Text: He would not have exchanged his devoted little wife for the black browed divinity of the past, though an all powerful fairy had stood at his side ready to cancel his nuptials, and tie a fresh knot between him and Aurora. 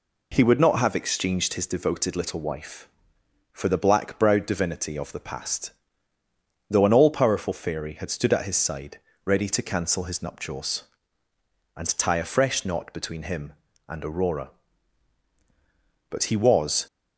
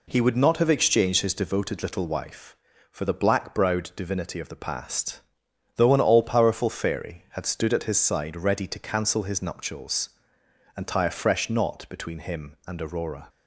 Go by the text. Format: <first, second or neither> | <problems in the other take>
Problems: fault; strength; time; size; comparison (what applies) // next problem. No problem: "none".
second | pauses between "side" and "ready"; slight; at 8.9 s; 0.30 s long // goes on to say "But he was"; noticeable; from 16.0 s on; 0.78 s long